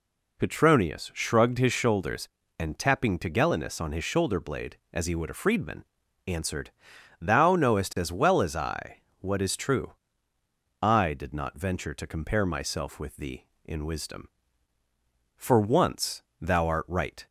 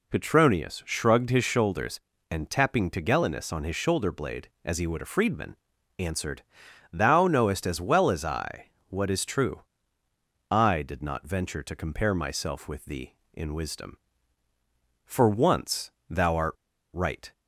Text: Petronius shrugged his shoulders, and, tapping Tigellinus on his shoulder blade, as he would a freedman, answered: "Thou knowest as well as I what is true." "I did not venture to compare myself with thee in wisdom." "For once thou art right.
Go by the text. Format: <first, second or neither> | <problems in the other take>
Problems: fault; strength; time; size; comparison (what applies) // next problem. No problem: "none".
first | pauses between "I" and "what"; slight; at 8.7 s; 0.16 s long; slight in the first // pauses between "once" and "thou"; slight; at 15.9 s; 0.18 s long; slight in the first // pauses between "art" and "right"; at 16.5 s; 0.38 s long